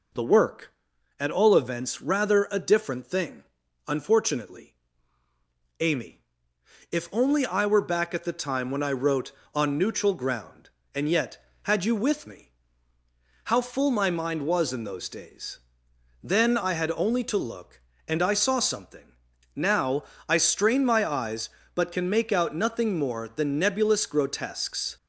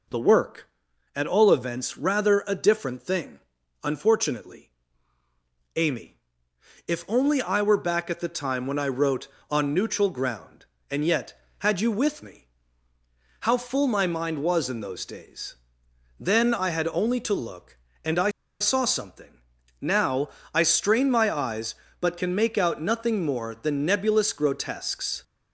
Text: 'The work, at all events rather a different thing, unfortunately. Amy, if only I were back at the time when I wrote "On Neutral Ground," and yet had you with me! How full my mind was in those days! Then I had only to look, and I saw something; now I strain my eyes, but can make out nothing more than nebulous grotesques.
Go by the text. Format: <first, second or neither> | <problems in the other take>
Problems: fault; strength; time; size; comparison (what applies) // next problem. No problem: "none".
first | pauses between "I" and "saw"; slight; at 18.2 s; 0.30 s long // pauses between "now" and "I"; slight; at 20.2 s; 0.24 s long; slight in the first